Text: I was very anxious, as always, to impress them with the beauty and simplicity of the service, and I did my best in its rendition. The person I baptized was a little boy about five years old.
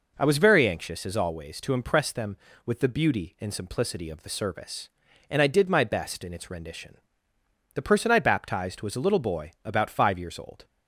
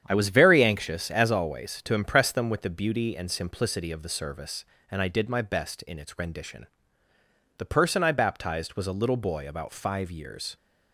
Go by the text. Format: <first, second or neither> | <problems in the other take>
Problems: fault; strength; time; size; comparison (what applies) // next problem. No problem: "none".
first | starts louder than the rest; strong; until 1.0 s; 9 dB // stops before "old"; at 10.5 s